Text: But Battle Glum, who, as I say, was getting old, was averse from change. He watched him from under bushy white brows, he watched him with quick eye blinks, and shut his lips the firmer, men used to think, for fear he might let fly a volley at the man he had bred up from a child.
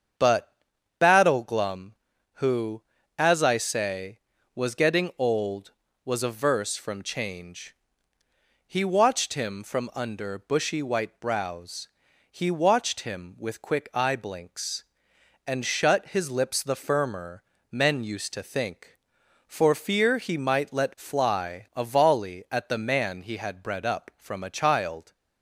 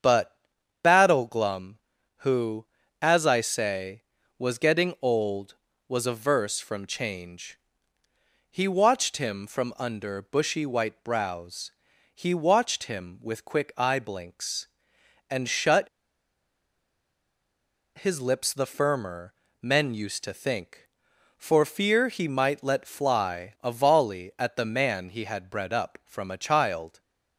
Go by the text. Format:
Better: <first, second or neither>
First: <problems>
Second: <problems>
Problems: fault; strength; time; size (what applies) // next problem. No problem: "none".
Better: first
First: starts louder than the rest; strong; until 1.6 s; 7.5 dB // pauses between "But" and "Battle"; noticeable; at 0.5 s; 0.46 s long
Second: starts louder than the rest; strong; until 1.4 s; 7.5 dB // pauses between "But" and "Battle"; noticeable; at 0.3 s; 0.46 s long // pauses between "shut" and "his"; strong; at 15.8 s; 2.0 s long